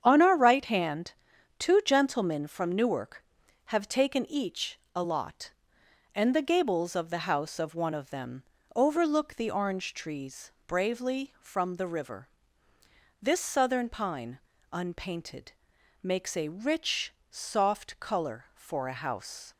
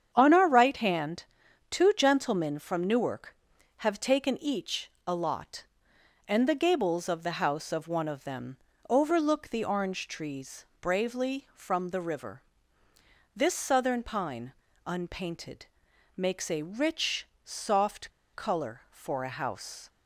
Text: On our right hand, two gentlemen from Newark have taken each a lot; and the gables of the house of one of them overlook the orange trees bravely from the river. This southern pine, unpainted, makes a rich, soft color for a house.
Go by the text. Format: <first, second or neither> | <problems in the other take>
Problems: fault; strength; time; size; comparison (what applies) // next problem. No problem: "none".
first | starts louder than the rest; strong; until 1.1 s; 8 dB; strong in the first // pauses between "each" and "a"; slight; at 4.9 s; 0.16 s long; slight in the first // pauses between "them" and "overlook"; slight; at 8.5 s; 0.32 s long; slight in the first // pauses between "trees" and "bravely"; slight; at 10.6 s; 0.16 s long; slight in the first // pauses between "soft" and "color"; slight; at 18.1 s; 0.23 s long